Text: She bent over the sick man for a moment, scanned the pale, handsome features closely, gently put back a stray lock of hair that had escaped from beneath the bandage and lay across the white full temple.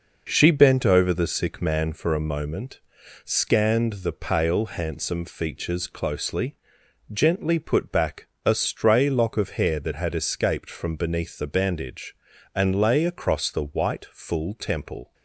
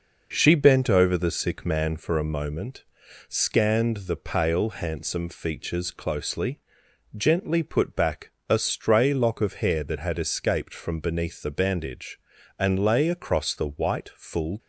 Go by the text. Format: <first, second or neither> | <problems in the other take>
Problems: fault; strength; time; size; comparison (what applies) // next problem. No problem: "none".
first | pauses between "back" and "a"; slight; at 8.2 s; 0.18 s long; slight in the first // stops before "temple"; at 14.5 s